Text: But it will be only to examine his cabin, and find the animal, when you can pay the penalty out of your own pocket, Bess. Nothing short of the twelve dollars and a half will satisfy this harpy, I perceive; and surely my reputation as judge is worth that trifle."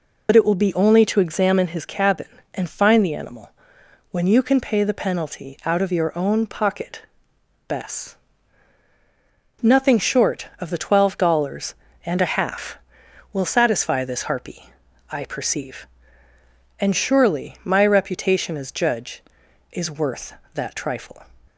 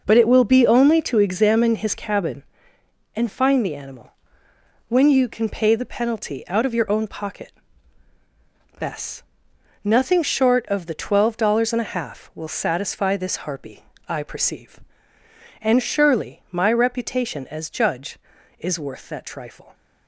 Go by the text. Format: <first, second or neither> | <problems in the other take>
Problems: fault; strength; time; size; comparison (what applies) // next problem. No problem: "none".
second | loses the start of "But"; at 0.2 s; 55 ms